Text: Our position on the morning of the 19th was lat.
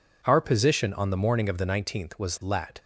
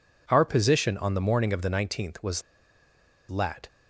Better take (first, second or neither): first